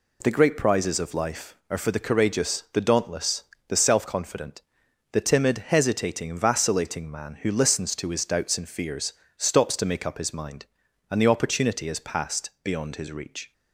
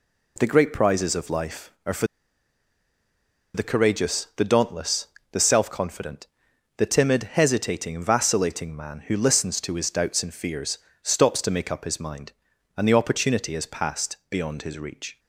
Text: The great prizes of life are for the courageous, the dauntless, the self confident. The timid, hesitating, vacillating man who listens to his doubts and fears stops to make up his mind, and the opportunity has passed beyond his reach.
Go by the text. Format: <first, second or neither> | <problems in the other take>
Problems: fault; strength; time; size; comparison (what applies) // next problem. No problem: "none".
first | pauses between "for" and "the"; strong; at 2.0 s; 1.4 s long // pauses between "fears" and "stops"; slight; at 10.7 s; 0.24 s long; slight in the first